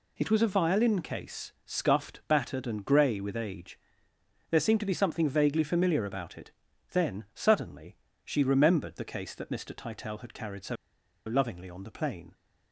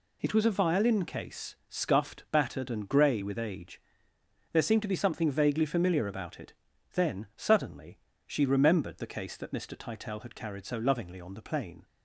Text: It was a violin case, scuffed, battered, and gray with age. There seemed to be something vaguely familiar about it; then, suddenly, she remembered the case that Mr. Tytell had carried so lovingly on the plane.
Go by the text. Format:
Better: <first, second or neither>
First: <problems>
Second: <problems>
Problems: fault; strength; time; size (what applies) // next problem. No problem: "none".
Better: second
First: pauses between "so" and "lovingly"; noticeable; at 10.7 s; 0.51 s long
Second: none